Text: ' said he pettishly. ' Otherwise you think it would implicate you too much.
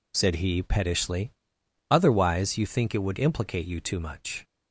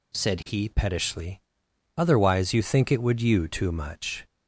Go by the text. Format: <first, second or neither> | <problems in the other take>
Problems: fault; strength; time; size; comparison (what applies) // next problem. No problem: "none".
first | skips "implicate"; at 3.2 s